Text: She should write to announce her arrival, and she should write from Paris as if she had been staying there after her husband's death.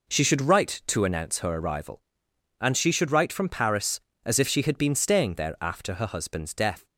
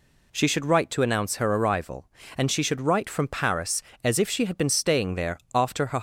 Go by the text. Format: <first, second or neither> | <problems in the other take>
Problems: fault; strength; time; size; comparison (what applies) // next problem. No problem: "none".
first | pauses between "there" and "after"; slight; at 5.3 s; 0.16 s long // stops before "husband's death"; at 5.9 s